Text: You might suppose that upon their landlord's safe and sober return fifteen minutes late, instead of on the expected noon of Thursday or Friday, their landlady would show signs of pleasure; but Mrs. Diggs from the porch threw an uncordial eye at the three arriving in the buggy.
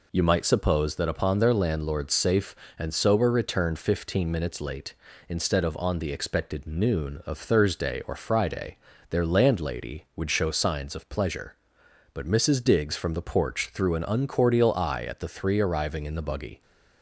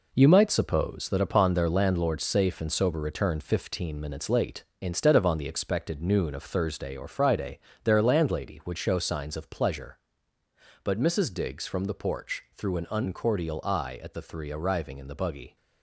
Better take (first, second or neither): first